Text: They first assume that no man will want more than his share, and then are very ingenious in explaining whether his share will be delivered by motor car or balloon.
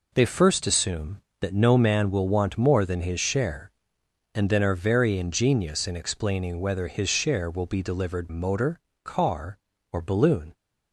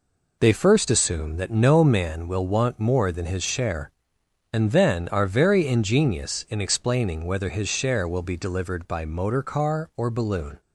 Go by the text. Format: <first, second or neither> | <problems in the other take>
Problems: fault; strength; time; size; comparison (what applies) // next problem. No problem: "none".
second | skips "by"; at 8.2 s // pauses between "motor" and "car"; slight; at 8.8 s; 0.22 s long